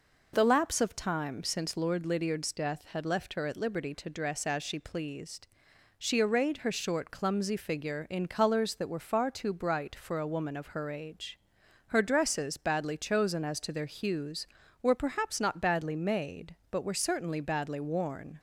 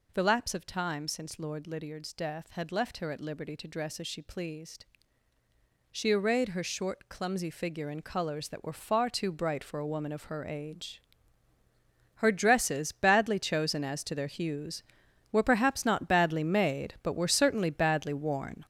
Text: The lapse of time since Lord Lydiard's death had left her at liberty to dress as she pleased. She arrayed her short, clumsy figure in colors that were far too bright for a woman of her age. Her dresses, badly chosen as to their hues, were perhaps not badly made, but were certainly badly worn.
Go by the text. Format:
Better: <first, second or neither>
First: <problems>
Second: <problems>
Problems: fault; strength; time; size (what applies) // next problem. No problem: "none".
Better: first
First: none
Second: gets louder; strong; throughout; 8 dB